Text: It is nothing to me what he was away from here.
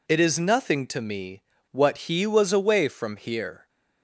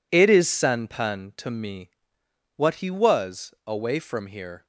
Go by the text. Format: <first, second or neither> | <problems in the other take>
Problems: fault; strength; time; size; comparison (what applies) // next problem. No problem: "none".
first | says "sanpan" for "nothing"; at 0.4 s // pauses between "me" and "what"; noticeable; at 1.9 s; 0.64 s long; slight in the first